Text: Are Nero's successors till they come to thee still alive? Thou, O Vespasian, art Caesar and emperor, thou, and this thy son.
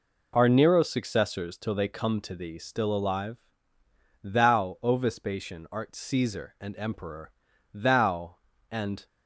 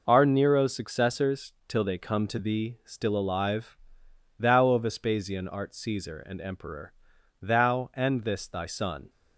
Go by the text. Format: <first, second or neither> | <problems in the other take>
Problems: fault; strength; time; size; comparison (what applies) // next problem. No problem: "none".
second | stops before "this thy son"; at 9.0 s